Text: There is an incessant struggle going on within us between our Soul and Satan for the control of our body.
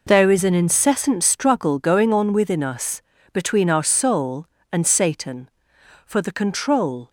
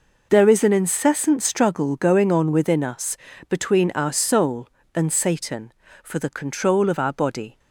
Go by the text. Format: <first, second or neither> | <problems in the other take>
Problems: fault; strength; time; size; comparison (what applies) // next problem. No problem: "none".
second | pauses between "us" and "between"; slight; at 3.0 s; 0.32 s long; slight in the second // stops before "of our body"; at 7.0 s